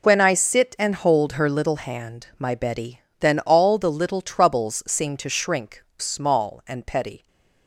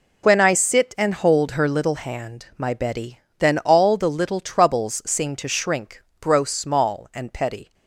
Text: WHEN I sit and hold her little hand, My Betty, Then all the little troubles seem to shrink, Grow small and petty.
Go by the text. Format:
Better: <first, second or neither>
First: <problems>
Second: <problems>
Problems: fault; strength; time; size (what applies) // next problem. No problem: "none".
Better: second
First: skips "Grow"; at 5.9 s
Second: none